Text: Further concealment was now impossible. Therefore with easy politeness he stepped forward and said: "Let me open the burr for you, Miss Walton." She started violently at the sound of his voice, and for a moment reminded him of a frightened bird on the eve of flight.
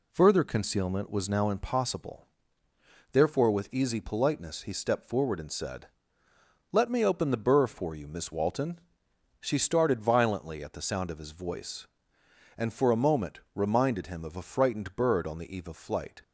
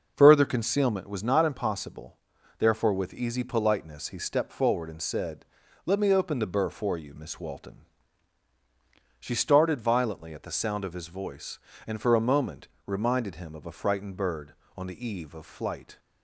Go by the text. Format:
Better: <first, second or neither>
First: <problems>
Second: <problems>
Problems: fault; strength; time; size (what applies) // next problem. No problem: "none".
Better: first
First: pauses between "moment" and "reminded"; slight; at 13.3 s; 0.16 s long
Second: says "not" for "now"; at 1.2 s // pauses between "moment" and "reminded"; slight; at 12.6 s; 0.18 s long